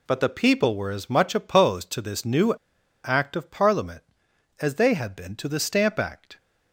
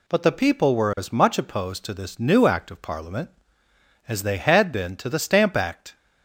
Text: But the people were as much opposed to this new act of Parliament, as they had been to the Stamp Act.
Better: second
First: pauses between "new" and "act"; noticeable; at 2.5 s; 0.50 s long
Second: none

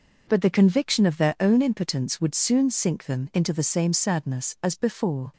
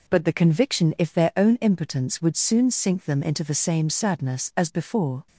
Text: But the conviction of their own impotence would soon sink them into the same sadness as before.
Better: first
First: none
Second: says "if" for "of"; at 0.9 s

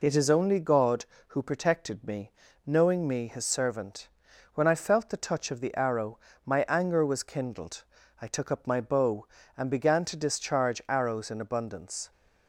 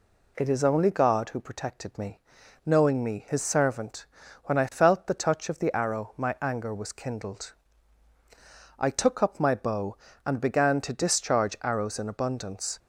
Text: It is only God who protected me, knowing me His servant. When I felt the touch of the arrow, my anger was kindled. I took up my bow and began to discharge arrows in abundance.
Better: neither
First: none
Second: none

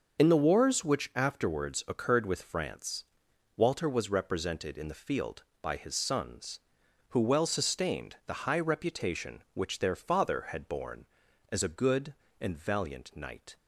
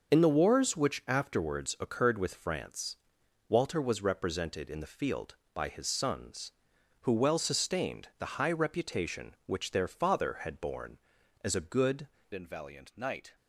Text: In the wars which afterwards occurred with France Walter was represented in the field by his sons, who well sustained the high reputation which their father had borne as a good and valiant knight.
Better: first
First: starts louder than the rest; until 1.2 s; 6 dB // pauses between "France" and "Walter"; noticeable; at 3.0 s; 0.52 s long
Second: starts louder than the rest; until 1.1 s; 6 dB // pauses between "France" and "Walter"; noticeable; at 2.9 s; 0.52 s long // changes voice at "and"; from 12.3 s on; 1.0 s long

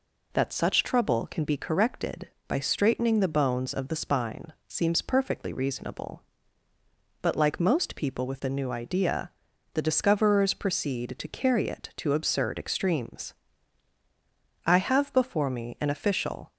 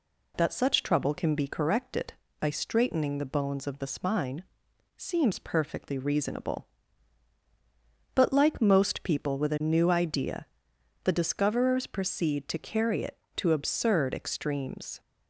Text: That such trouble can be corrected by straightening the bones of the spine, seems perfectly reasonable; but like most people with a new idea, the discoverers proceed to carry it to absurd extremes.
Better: second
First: goes on to say "I have before me an official"; strong; from 14.6 s on; 1.8 s long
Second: none

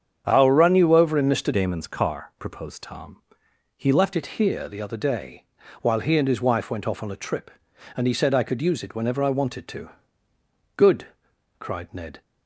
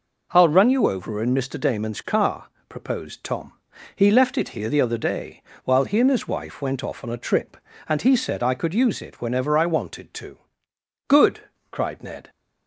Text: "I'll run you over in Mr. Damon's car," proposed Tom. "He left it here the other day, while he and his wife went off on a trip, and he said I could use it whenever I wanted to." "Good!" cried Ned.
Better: second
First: starts louder than the rest; strong; until 1.2 s; 8 dB // changes voice from "Damon's" to "left"; from 1.5 to 4.1 s; 2.6 s long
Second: none

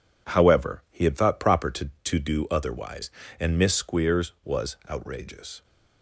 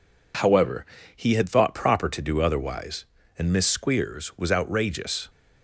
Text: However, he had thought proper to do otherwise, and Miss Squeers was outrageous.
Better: second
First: says "to" twice; at 2.0 s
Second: none

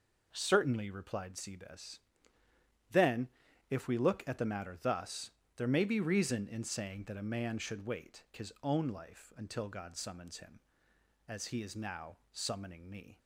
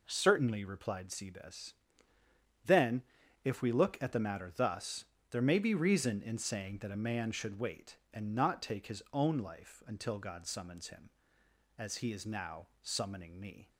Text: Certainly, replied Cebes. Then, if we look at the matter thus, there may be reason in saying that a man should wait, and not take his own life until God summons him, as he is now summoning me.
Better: second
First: skips "and not take"; at 8.3 s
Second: none

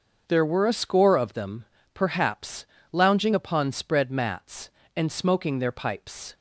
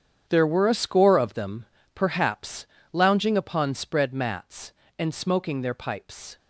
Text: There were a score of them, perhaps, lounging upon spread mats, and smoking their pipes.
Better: first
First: starts louder than the rest; until 1.2 s; 6.5 dB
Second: gets quieter; strong; throughout; 13.5 dB // starts louder than the rest; strong; until 1.3 s; 8.5 dB

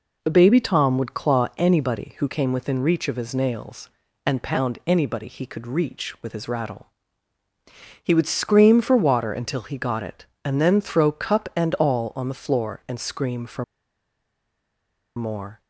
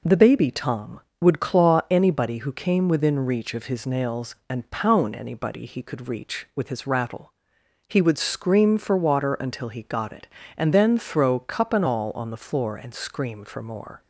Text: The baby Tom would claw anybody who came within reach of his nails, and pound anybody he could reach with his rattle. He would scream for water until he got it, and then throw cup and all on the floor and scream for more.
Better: second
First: pauses between "for" and "more"; strong; at 13.6 s; 1.5 s long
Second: none

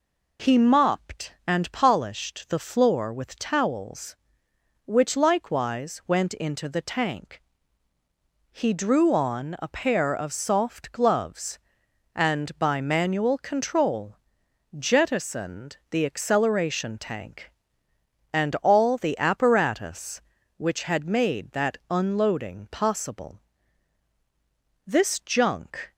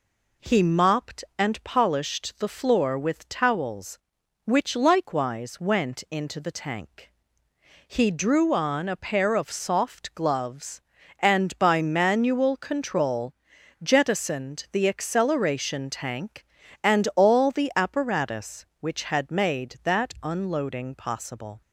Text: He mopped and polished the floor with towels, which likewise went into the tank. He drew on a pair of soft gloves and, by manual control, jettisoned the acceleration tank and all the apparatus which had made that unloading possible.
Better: second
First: goes on to say "This junk"; noticeable; from 24.8 s on; 1.0 s long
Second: none

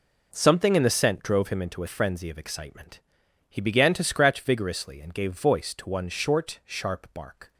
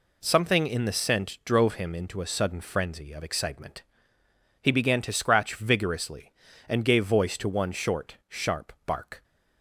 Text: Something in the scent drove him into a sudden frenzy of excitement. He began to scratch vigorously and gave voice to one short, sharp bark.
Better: second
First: skips "sudden"; at 1.8 s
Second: none

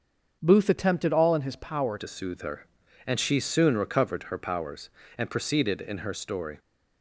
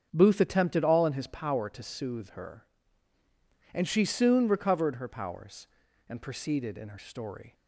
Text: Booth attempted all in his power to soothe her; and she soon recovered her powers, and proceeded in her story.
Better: second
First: starts louder than the rest; until 1.4 s; 7 dB // changes voice at "to"; from 1.9 s on; 4.6 s long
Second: starts louder than the rest; strong; until 1.1 s; 7 dB

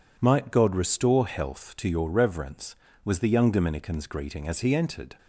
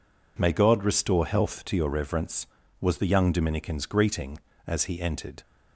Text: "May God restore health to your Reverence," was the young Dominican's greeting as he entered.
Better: second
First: says "Might" for "May"; at 0.1 s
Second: none

